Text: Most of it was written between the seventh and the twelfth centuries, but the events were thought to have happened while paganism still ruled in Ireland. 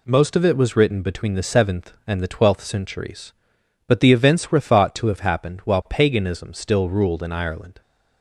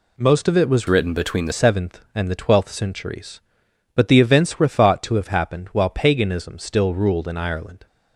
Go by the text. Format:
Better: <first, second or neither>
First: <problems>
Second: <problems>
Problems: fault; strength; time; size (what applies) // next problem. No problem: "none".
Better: first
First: none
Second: changes voice from "written" to "the"; from 0.8 to 1.5 s; 0.7 s long